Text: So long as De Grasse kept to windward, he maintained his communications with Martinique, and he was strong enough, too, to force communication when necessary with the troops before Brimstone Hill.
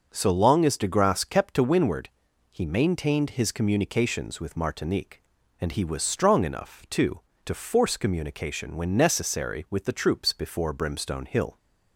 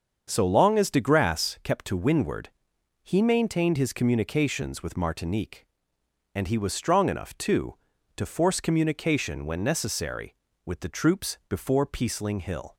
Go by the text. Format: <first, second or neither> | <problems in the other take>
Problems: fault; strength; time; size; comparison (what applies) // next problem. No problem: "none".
first | starts louder than the rest; until 1.3 s; 7 dB // says "Peaceling" for "Brimstone"; at 11.8 s